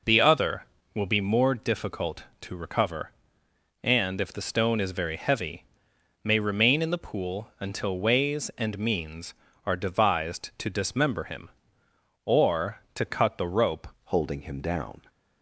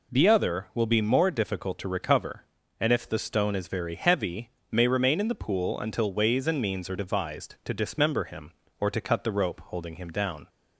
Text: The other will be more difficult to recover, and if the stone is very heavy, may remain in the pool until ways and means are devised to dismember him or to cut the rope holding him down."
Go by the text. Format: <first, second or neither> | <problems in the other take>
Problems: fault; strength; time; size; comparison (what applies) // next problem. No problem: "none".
second | changes voice at "holding"; from 14.0 s on; 1.0 s long